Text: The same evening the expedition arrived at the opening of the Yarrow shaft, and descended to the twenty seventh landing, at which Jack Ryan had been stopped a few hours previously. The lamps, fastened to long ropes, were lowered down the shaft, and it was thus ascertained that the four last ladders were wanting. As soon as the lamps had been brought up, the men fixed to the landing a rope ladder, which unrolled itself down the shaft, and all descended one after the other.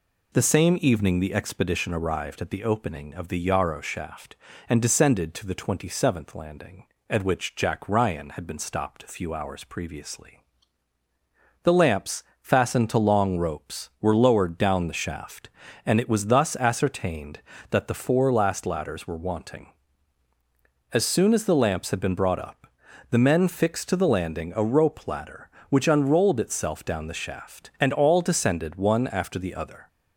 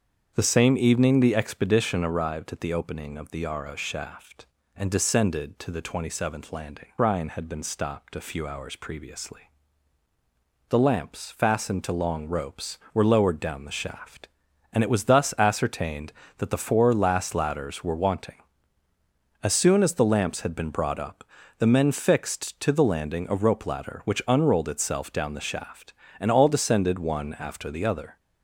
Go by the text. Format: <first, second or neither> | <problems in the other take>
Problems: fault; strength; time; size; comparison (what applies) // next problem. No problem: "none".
first | starts louder than the rest; strong; until 1.3 s; 7 dB // skips "at which Jack"; at 6.9 s